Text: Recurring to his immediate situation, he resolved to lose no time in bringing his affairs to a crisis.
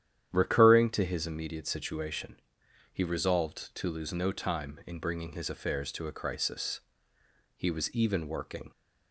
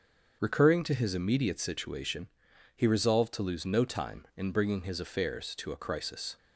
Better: second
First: starts louder than the rest; strong; until 1.3 s; 10 dB // goes on to say "He was even working"; noticeable; from 7.5 s on; 1.1 s long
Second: starts louder than the rest; until 1.4 s; 6.5 dB

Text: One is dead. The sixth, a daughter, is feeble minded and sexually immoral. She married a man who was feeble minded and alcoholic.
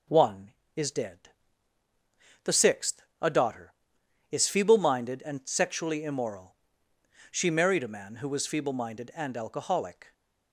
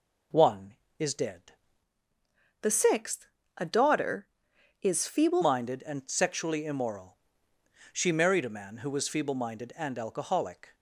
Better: first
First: none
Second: changes voice from "The" to "feeble"; from 2.6 to 5.4 s; 2.8 s long

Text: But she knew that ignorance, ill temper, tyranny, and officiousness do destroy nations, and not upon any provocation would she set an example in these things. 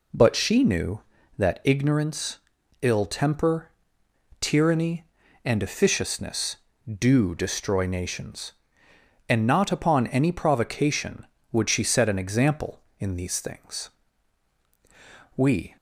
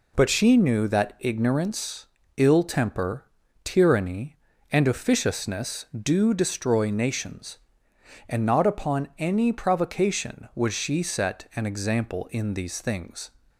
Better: second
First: goes on to say "We"; slight; from 15.3 s on; 0.40 s long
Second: none

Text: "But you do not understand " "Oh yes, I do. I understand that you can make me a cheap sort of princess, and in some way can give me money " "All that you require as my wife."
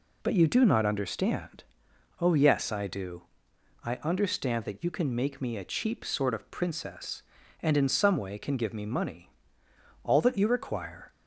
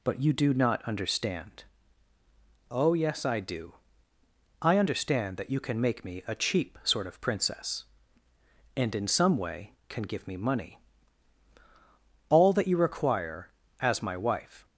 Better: second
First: stops before "as my wife"; at 11.1 s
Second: none

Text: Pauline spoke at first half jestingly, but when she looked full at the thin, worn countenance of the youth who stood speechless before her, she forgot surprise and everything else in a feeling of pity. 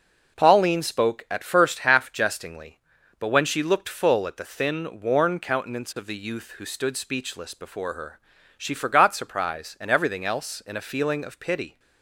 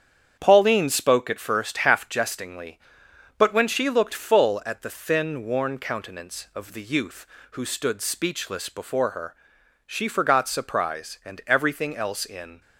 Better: first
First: none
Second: starts louder than the rest; strong; until 1.4 s; 8.5 dB // stops before "a feeling of pity"; at 12.6 s

